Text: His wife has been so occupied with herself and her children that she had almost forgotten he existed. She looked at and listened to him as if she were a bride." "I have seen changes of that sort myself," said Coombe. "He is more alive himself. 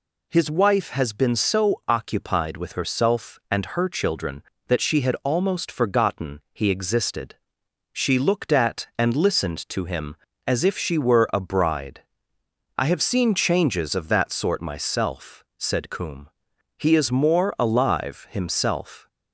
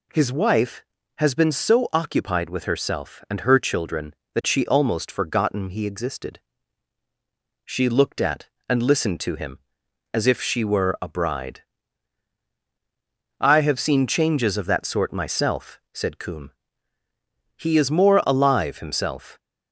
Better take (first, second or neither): first